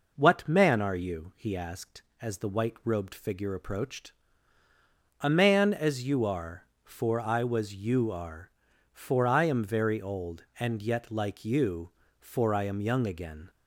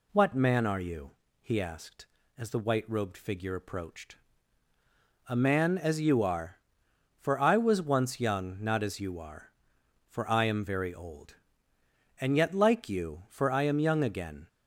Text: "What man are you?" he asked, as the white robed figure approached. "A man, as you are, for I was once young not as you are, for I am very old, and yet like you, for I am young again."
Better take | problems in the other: second | skips "once young not as"; at 7.7 s

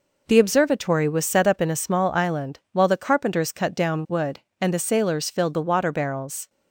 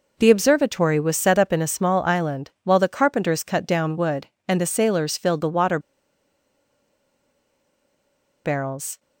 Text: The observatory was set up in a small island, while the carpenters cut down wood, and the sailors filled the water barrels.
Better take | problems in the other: first | pauses between "water" and "barrels"; strong; at 5.7 s; 2.6 s long

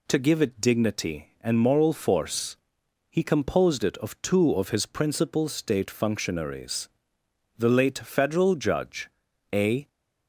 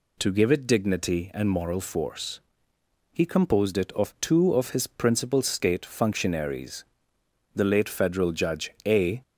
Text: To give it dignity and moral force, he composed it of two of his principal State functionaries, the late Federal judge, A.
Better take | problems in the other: neither | none

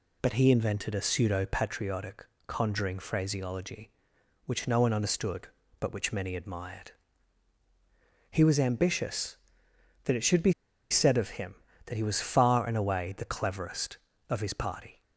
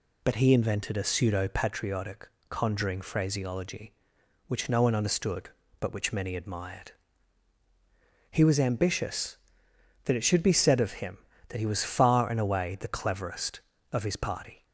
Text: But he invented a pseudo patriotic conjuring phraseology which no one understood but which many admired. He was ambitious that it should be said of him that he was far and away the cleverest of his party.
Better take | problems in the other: second | pauses between "patriotic" and "conjuring"; slight; at 2.2 s; 0.20 s long; slight in the second // pauses between "be" and "said"; at 10.5 s; 0.38 s long

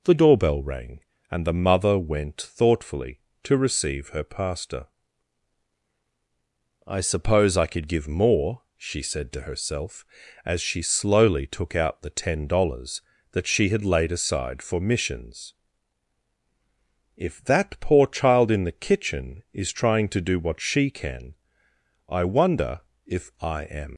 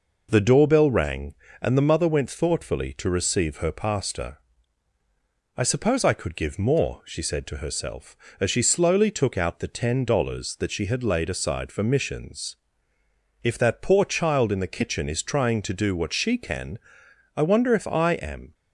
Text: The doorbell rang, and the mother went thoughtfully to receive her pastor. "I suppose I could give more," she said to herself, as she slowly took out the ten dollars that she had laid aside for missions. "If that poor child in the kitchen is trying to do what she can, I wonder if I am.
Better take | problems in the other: second | pauses between "wonder" and "if"; slight; at 22.7 s; 0.24 s long // leaves "am" unfinished; at 23.9 s; 95 ms

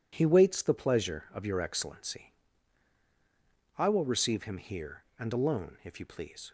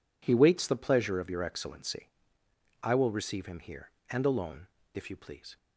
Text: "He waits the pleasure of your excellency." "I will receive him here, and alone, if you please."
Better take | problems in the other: neither | none

